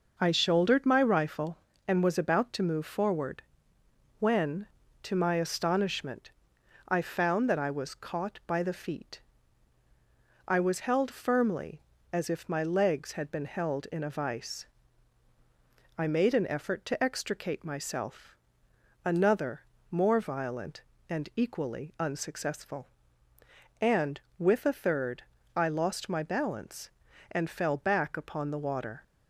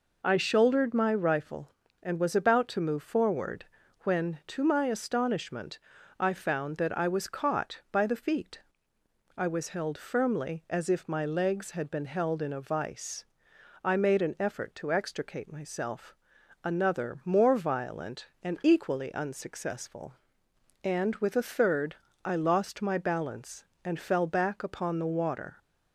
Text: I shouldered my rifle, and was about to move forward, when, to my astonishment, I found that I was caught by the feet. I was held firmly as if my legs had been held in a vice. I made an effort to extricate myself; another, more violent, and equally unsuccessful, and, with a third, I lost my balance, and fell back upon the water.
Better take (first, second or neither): neither